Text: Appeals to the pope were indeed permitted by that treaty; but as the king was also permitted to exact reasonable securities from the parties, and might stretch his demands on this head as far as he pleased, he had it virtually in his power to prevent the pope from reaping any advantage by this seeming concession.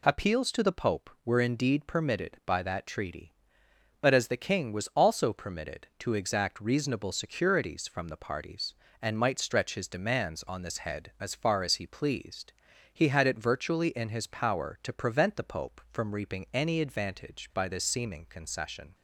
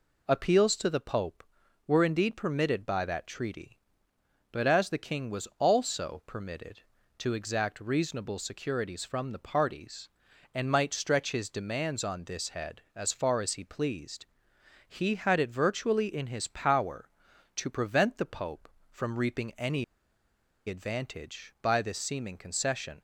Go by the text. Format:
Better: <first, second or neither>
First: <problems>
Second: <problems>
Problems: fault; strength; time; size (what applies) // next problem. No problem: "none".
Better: first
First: none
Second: pauses between "any" and "advantage"; noticeable; at 19.8 s; 0.83 s long